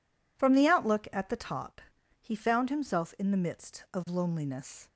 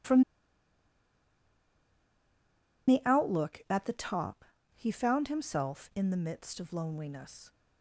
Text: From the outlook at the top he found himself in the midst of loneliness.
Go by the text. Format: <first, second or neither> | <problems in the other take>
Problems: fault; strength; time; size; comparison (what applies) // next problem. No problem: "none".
first | pauses between "From" and "the"; strong; at 0.2 s; 2.6 s long // pauses between "top" and "he"; slight; at 4.4 s; 0.32 s long; also in the first